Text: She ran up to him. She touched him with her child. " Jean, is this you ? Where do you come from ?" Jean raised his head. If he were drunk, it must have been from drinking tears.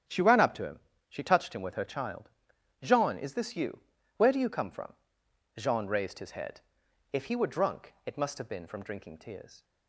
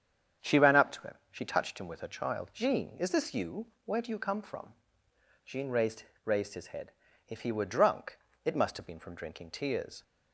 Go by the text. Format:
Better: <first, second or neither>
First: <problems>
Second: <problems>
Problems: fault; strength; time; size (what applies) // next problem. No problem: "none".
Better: first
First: starts louder than the rest; strong; until 1.3 s; 8.5 dB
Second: starts louder than the rest; strong; until 1.6 s; 8.5 dB // says "raised" twice; at 6.2 s